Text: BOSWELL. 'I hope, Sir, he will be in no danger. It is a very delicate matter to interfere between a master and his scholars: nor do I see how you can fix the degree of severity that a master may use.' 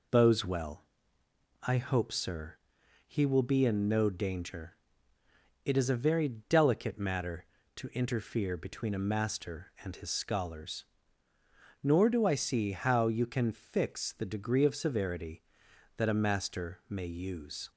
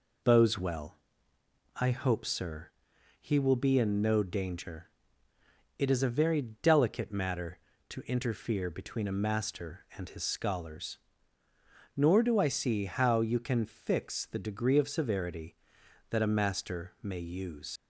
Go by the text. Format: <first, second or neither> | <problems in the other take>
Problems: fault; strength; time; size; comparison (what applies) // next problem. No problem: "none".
first | leaves "use" unfinished; at 17.7 s; 75 ms